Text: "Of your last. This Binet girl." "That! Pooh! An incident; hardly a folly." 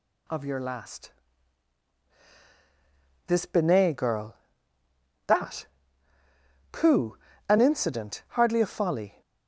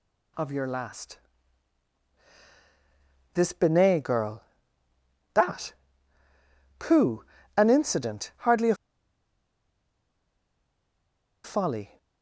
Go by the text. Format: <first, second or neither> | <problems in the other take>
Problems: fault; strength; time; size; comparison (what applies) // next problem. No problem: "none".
first | pauses between "a" and "folly"; strong; at 8.7 s; 2.6 s long